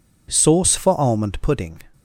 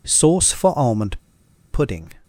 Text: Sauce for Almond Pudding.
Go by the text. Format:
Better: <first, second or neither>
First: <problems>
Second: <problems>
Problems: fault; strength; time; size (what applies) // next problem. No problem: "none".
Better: first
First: none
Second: pauses between "Almond" and "Pudding"; noticeable; at 1.1 s; 0.53 s long